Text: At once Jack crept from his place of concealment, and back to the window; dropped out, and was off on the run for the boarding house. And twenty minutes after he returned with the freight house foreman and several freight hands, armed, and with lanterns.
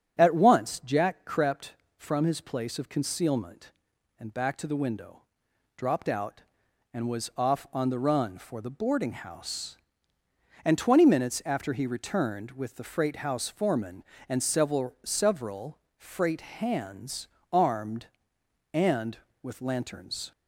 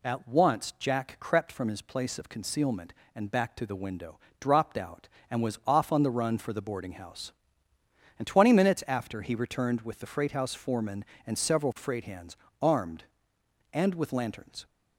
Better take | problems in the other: second | starts louder than the rest; strong; until 1.2 s; 8.5 dB // says "several" twice; at 15.0 s

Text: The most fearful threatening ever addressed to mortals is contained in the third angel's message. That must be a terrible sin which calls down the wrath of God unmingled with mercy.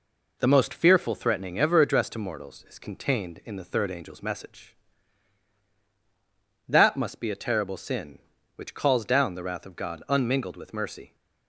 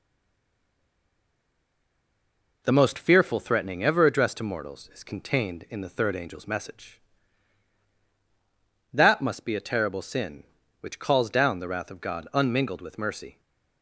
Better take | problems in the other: first | stays silent before the first word; strong; until 2.6 s; 2.6 s long

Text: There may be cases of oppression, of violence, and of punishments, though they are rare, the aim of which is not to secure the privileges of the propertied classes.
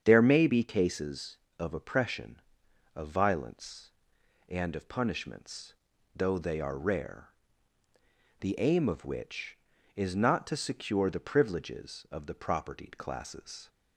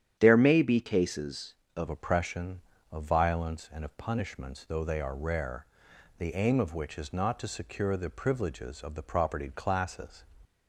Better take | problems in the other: first | starts louder than the rest; strong; until 1.2 s; 9.5 dB; strong in the first // changes voice at "oppression"; from 1.8 s on; 8.4 s long

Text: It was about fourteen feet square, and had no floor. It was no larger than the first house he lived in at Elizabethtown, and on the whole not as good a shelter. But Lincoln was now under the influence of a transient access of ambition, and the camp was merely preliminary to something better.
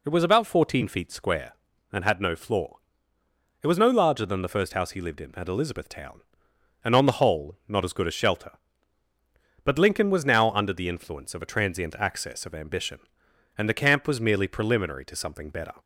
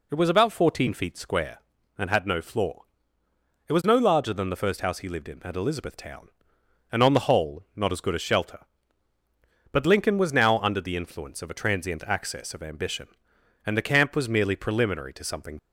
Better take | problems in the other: first | stops before "better"; at 15.5 s

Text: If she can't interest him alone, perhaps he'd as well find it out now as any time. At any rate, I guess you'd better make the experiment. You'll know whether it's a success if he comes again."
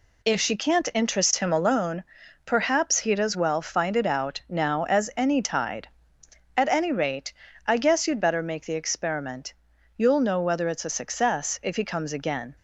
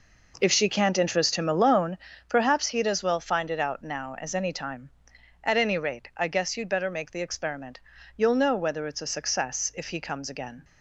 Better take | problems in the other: second | says "tide" for "time"; at 5.4 s

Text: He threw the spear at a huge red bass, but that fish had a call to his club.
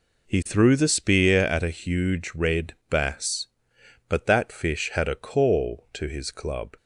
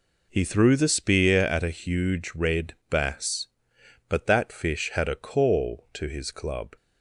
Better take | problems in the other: neither | pauses between "red" and "bass"; slight; the same in both

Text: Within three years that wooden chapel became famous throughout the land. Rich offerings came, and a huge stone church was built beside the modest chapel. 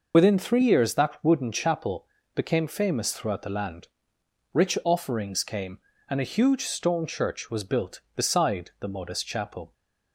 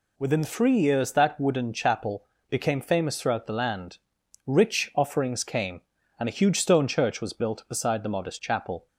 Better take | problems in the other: second | loses the start of "Within"; at 0.1 s; 45 ms // pauses between "chapel" and "became"; slight; at 2.0 s; 0.30 s long; slight in the second

